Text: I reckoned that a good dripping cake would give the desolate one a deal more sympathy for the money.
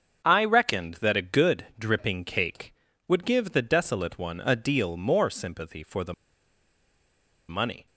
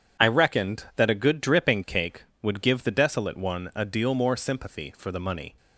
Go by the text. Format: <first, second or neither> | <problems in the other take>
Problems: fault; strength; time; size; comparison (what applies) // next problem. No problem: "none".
second | starts louder than the rest; until 1.2 s; 6.5 dB // pauses between "the" and "money"; strong; at 6.1 s; 1.3 s long